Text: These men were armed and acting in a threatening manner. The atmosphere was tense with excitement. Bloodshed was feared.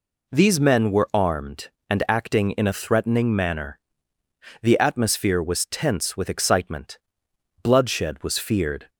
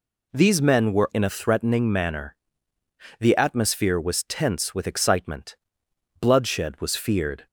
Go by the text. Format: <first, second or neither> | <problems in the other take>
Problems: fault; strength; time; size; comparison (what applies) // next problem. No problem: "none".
first | skips "armed and acting"; at 1.1 s